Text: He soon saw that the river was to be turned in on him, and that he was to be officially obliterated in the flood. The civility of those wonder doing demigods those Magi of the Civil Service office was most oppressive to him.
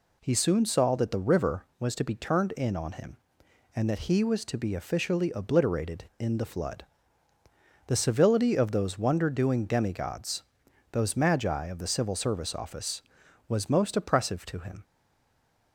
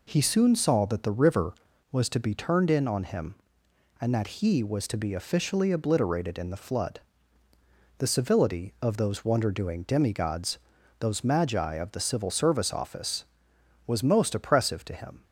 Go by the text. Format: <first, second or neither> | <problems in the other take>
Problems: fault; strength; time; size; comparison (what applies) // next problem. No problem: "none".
second | pauses between "demigods" and "those"; noticeable; at 10.4 s; 0.48 s long; also in the second // stays silent after the last word; slight; from 14.8 s on; 0.9 s long